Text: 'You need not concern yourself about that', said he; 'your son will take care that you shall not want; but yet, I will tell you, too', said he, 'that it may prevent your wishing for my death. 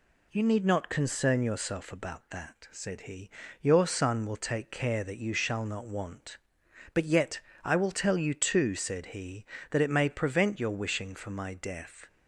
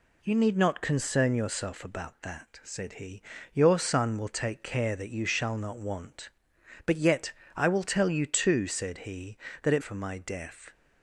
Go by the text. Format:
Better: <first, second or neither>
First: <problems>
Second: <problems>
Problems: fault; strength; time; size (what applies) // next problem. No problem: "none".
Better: first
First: none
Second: skips "may prevent your wishing"; at 9.8 s